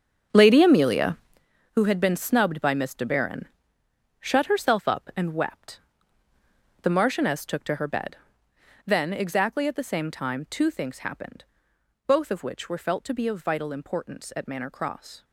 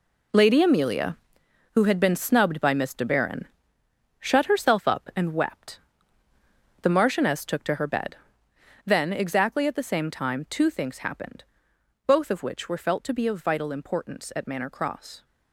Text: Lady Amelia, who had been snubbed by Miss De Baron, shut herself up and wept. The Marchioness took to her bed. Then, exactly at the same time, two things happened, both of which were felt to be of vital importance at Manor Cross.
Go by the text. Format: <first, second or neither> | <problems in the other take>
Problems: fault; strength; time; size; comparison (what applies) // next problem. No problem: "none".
second | starts louder than the rest; strong; until 1.5 s; 7.5 dB